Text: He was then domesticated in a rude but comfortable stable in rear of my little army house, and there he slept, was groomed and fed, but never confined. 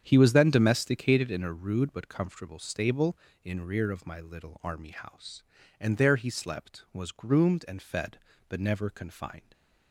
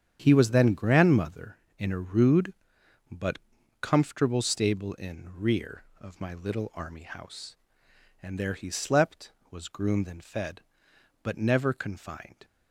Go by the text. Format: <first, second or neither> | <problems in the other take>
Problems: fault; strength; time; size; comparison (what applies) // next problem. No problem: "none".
first | starts louder than the rest; strong; until 1.2 s; 8.5 dB; strong in the first // says "grandmother" for "domesticated"; at 0.7 s // pauses between "but" and "comfortable"; at 3.3 s; 0.42 s long